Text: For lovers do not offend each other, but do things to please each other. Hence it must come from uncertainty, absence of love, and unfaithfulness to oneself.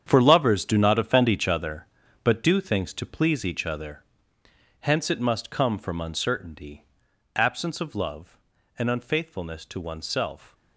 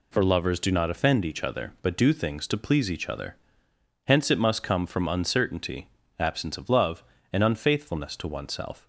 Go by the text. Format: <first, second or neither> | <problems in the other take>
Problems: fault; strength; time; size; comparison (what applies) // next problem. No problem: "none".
second | gets quieter; strong; throughout; 12.5 dB